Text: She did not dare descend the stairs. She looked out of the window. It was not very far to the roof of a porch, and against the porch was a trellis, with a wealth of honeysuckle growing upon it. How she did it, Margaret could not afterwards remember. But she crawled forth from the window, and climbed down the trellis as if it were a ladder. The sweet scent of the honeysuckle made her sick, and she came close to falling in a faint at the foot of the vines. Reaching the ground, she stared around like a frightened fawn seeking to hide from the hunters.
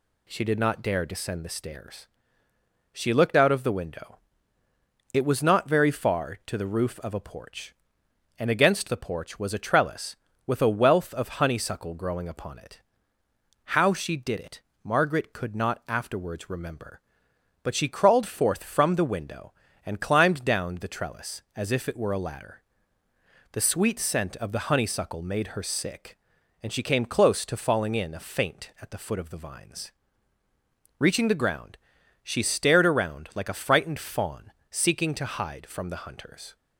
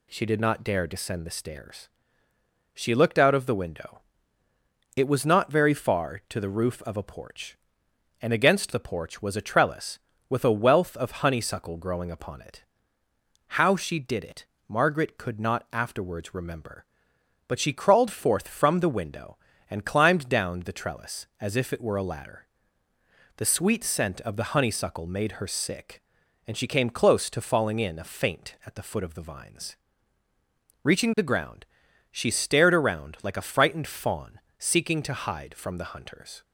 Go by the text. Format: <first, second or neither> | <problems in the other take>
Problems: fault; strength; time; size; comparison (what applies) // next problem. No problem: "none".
neither | pauses between "fawn" and "seeking"; slight; the same in both